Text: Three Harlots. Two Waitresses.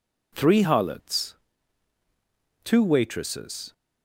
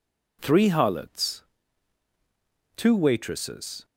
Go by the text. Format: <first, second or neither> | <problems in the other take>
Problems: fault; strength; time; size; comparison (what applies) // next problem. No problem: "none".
neither | none